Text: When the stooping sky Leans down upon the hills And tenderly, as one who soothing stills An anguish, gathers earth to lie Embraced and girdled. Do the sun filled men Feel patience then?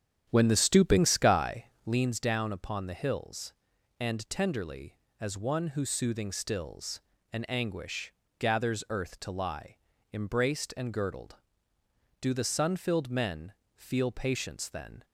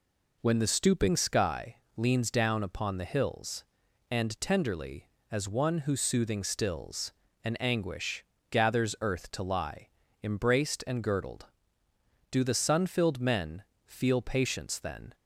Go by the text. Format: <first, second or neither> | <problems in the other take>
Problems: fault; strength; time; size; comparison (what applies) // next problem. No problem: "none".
second | starts louder than the rest; strong; until 2.1 s; 9 dB // pauses between "sky" and "Leans"; slight; at 1.6 s; 0.20 s long; slight in the second // pauses between "stills" and "An"; slight; at 7.0 s; 0.32 s long; slight in the second // pauses between "lie" and "Embraced"; slight; at 9.7 s; 0.36 s long; slight in the second // pauses between "men" and "Feel"; slight; at 13.5 s; 0.24 s long; slight in the second